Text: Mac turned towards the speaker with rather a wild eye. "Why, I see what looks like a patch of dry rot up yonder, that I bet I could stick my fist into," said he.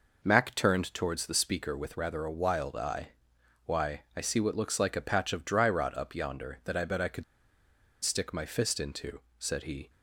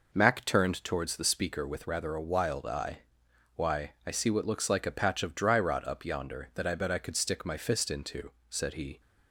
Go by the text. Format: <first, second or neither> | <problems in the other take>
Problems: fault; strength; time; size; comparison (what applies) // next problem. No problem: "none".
second | pauses between "could" and "stick"; noticeable; at 7.2 s; 0.79 s long